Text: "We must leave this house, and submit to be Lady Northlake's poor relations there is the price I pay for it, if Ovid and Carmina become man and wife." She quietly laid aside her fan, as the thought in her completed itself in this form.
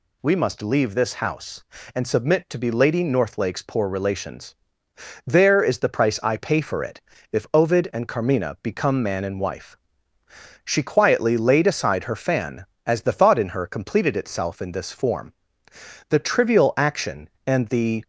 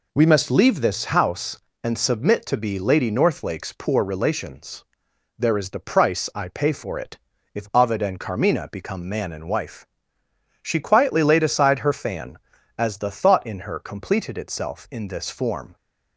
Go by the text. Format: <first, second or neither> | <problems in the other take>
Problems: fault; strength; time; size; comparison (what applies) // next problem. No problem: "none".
second | pauses between "relations" and "there"; noticeable; at 4.5 s; 0.72 s long; noticeable in the second // goes on to say "The trivial action and the"; strong; from 16.0 s on; 1.9 s long